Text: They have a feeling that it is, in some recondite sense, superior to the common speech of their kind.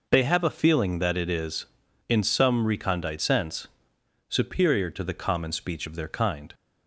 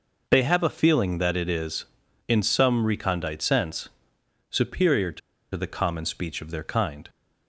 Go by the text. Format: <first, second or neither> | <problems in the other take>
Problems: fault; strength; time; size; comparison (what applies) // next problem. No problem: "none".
first | pauses between "to" and "the"; slight; at 5.2 s; 0.34 s long